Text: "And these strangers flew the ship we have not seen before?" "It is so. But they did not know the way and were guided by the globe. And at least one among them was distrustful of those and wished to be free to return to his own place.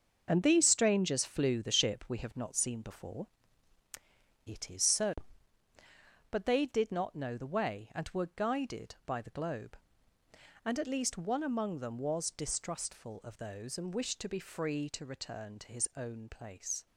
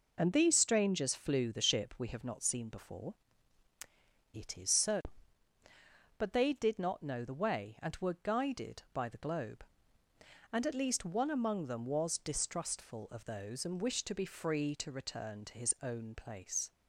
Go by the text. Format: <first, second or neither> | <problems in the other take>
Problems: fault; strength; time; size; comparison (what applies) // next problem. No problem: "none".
second | gets quieter; strong; throughout; 8.5 dB